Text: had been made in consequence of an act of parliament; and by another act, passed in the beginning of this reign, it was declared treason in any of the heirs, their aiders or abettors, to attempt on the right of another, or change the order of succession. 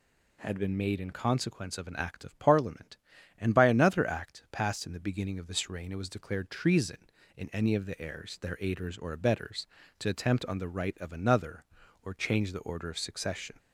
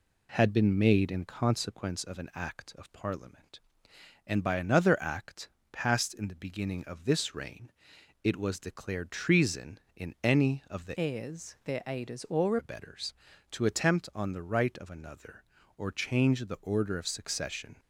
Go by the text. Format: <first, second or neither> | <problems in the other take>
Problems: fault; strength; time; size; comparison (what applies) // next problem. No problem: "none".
first | changes voice from "heirs" to "or"; from 10.9 to 12.5 s; 1.6 s long